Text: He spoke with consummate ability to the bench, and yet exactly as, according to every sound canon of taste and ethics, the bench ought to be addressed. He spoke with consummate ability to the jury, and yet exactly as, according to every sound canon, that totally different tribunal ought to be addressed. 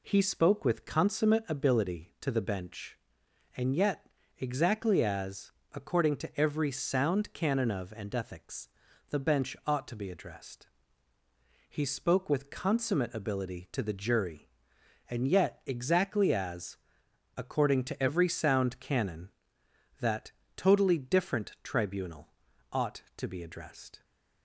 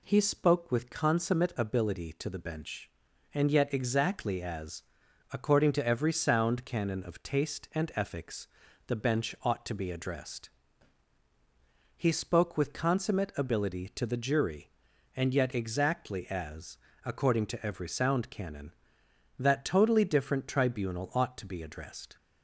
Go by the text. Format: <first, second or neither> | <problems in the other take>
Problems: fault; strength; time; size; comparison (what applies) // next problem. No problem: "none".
second | pauses between "yet" and "exactly"; slight; at 4.0 s; 0.32 s long // skips "taste"; at 7.9 s // pauses between "that" and "totally"; slight; at 20.3 s; 0.24 s long // pauses between "tribunal" and "ought"; noticeable; at 22.2 s; 0.46 s long